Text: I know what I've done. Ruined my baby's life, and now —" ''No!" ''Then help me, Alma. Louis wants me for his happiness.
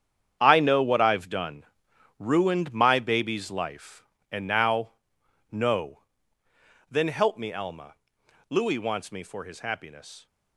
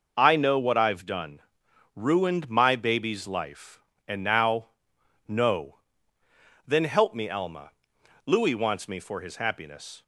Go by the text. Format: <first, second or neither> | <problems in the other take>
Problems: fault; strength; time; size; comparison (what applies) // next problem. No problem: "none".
second | gets quieter; strong; throughout; 13 dB